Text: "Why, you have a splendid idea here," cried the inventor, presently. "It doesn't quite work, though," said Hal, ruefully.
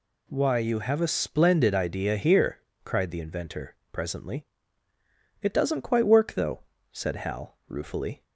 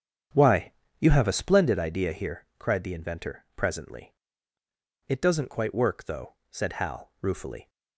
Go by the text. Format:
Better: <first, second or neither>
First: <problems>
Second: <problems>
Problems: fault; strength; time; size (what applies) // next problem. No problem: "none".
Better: first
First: none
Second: starts louder than the rest; strong; until 1.6 s; 8 dB